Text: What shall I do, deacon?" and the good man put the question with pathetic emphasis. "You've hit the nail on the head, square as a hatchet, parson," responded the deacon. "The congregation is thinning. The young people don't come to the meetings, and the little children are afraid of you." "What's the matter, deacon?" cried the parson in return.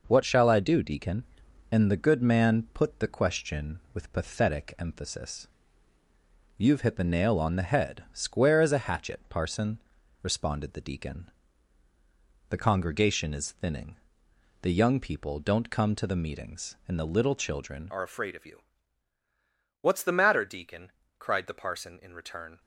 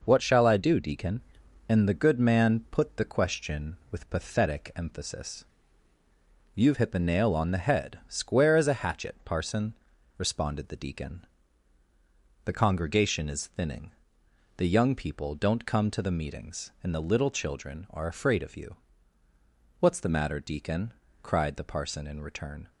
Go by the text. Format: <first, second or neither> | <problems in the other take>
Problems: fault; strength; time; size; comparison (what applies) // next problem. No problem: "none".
second | changes voice at "are"; from 17.9 s on; 4.6 s long